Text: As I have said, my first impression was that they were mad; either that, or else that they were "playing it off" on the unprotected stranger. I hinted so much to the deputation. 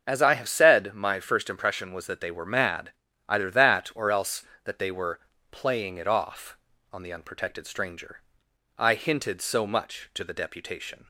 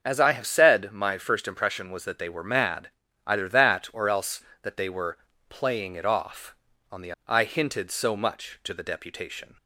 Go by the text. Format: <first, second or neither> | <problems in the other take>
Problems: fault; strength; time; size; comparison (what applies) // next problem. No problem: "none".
first | starts louder than the rest; until 1.0 s; 6.5 dB; also in the first // pauses between "were" and "playing"; slight; at 5.1 s; 0.32 s long; slight in the first // skips "unprotected stranger"; at 7.1 s